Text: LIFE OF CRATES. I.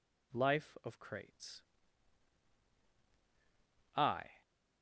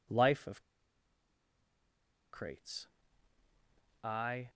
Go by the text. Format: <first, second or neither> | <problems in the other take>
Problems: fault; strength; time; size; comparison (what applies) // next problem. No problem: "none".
first | pauses between "OF" and "CRATES"; strong; at 0.6 s; 1.7 s long